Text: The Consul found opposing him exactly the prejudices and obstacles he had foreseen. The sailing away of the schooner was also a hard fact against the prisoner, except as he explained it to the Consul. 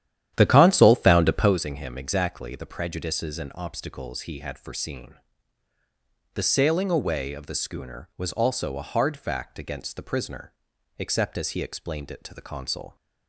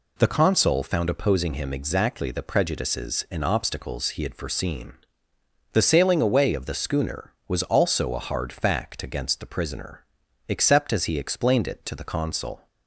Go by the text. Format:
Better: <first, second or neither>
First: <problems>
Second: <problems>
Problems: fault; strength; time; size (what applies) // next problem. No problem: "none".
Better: second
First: starts louder than the rest; strong; until 1.6 s; 11 dB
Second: none